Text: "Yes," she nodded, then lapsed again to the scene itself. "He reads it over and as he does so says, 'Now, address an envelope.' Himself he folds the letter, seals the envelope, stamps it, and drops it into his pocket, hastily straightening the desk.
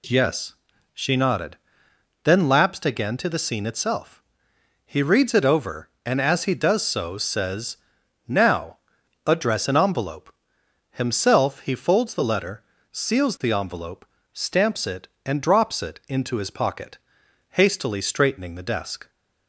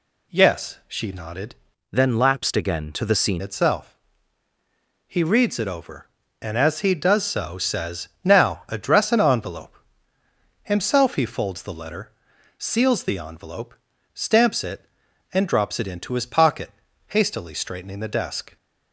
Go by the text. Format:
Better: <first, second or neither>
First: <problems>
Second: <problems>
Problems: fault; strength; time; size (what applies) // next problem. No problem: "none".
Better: first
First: none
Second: changes voice from "then" to "scene"; from 1.9 to 3.4 s; 1.5 s long